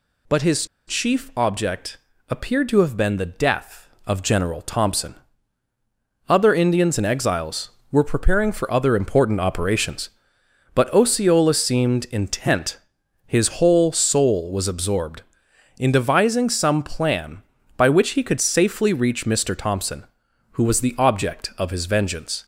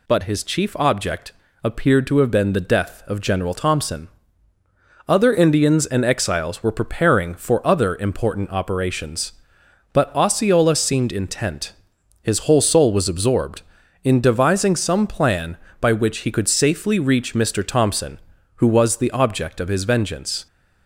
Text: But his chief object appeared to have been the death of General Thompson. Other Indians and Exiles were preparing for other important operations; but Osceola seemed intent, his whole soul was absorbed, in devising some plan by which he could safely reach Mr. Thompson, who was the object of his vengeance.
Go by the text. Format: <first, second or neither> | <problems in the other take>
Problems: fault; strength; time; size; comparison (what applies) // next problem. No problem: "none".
second | pauses between "his" and "chief"; slight; at 0.6 s; 0.22 s long // pauses between "object" and "appeared"; slight; at 1.9 s; 0.32 s long; slight in the second